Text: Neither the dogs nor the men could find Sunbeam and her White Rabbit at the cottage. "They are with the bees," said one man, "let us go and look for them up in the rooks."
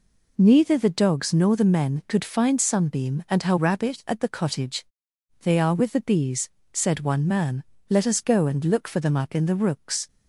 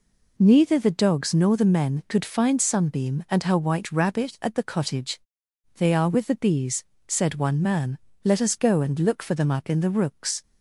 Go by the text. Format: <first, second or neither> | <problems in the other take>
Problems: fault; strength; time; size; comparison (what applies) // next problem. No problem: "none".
second | skips "White"; at 3.5 s